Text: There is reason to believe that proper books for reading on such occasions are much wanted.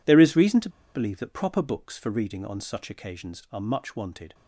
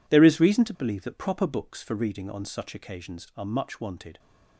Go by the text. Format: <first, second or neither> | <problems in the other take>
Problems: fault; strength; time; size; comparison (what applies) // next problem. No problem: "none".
second | pauses between "to" and "believe"; slight; at 0.6 s; 0.26 s long